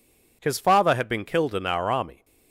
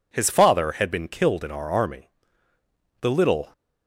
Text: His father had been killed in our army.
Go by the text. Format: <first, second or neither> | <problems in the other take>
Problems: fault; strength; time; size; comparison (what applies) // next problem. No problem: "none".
first | goes on to say "The little"; from 3.0 s on; 0.52 s long